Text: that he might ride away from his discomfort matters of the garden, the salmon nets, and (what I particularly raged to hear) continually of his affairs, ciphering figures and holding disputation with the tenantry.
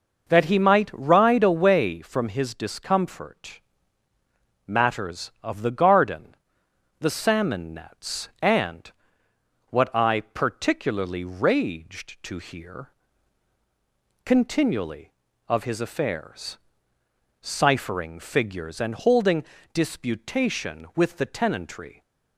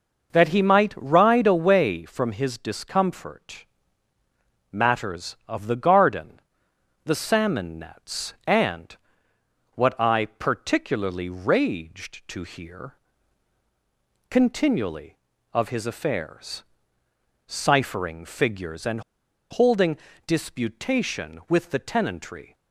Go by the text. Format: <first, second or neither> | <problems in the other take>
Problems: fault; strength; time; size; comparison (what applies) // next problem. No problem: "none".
first | pauses between "discomfort" and "matters"; at 3.6 s; 1.0 s long; also in the first // pauses between "and" and "holding"; noticeable; at 19.0 s; 0.49 s long // pauses between "holding" and "disputation"; slight; at 19.9 s; 0.28 s long; slight in the first